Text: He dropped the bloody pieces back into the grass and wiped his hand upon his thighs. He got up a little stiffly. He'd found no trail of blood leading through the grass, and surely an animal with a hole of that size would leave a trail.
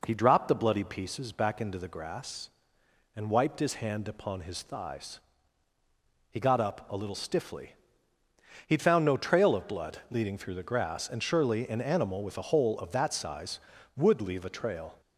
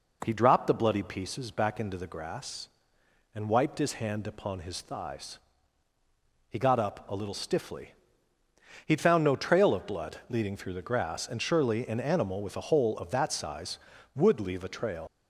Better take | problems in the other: first | leaves "trail" unfinished; at 15.0 s; 120 ms

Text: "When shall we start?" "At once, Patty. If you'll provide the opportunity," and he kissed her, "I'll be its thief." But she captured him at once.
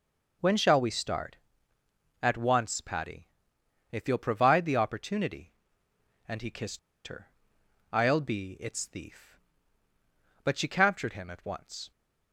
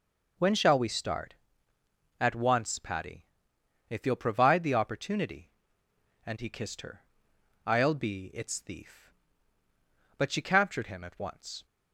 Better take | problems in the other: second | pauses between "kissed" and "her"; slight; at 6.7 s; 0.27 s long

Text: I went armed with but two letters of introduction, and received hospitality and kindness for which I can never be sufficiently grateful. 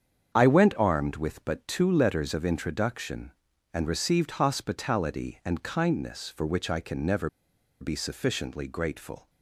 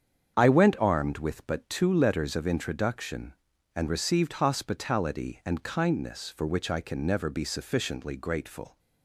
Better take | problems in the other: second | starts louder than the rest; strong; until 1.3 s; 8 dB; strong in the second // pauses between "never" and "be"; noticeable; at 7.2 s; 0.52 s long

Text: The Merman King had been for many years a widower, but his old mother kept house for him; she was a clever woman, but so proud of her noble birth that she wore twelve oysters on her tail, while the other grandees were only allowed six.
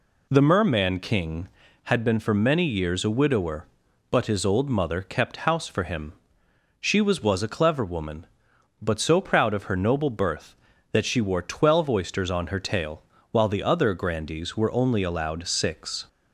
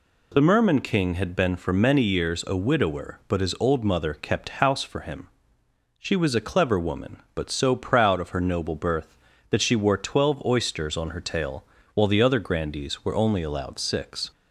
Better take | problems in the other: second | says "was" twice; at 7.2 s

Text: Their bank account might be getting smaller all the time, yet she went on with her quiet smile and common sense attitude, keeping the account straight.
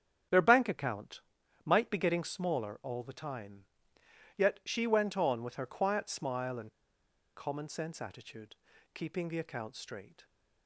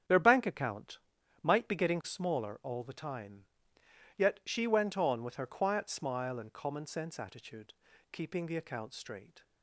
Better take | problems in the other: second | starts louder than the rest; strong; until 1.7 s; 9.5 dB; strong in the second // pauses between "account" and "might"; at 1.2 s; 0.44 s long; also in the second // pauses between "and" and "common"; noticeable; at 6.7 s; 0.65 s long

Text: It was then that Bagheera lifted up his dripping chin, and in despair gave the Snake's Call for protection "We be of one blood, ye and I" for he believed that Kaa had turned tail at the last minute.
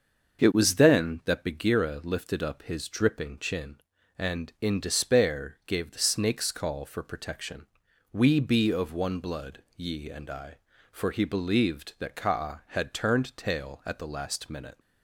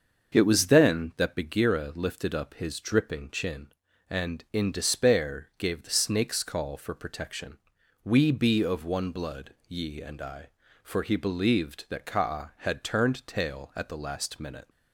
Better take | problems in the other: neither | starts louder than the rest; the same in both // pauses between "protection" and "We"; the same in both

